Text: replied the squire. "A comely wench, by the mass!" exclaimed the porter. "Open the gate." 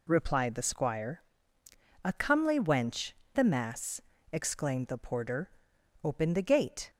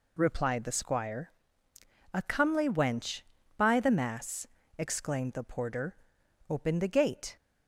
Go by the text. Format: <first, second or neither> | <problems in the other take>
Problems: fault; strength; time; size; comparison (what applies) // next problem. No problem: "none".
second | skips "by"; at 3.2 s